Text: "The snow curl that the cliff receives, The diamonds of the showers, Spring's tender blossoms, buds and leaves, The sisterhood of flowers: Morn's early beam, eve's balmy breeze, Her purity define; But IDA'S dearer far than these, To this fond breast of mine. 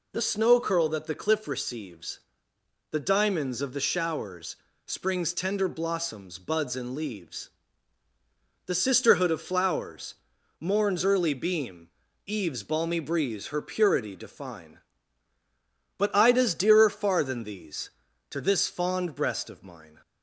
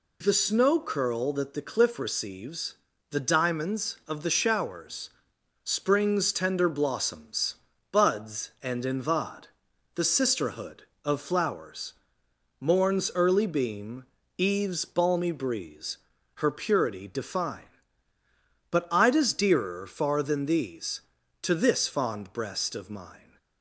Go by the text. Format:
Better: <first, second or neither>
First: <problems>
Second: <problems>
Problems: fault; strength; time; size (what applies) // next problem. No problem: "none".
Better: first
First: none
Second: says "invad" for "leaves"; at 8.8 s